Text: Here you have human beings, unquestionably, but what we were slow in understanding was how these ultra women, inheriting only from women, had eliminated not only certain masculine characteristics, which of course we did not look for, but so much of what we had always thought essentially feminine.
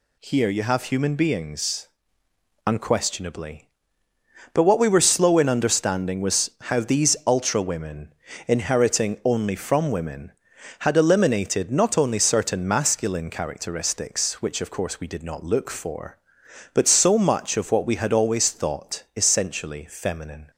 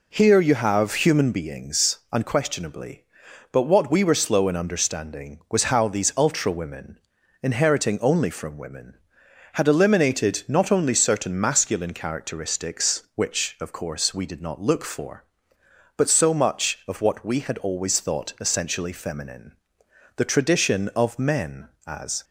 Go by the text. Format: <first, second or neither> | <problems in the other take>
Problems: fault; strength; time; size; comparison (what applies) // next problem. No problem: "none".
first | goes on to say "The tradition of men as"; strong; from 20.1 s on; 2.0 s long